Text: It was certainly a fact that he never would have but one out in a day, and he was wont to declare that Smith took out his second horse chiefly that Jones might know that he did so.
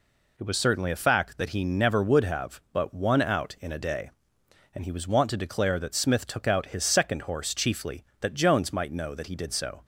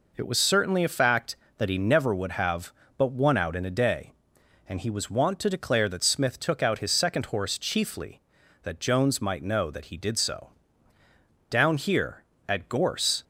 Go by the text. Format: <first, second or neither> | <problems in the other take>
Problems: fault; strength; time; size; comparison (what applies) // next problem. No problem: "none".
first | goes on to say "Down here at Gorse"; strong; from 11.4 s on; 1.7 s long